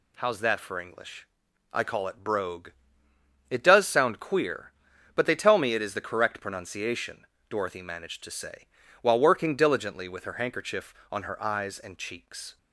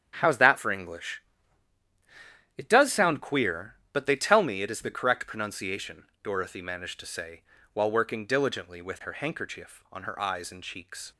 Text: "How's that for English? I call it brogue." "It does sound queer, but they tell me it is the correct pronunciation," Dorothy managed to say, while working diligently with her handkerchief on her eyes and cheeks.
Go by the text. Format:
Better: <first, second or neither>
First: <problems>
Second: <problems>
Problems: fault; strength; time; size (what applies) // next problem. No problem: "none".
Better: first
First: none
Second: starts louder than the rest; strong; until 1.1 s; 8.5 dB // skips "I call it brogue"; at 1.9 s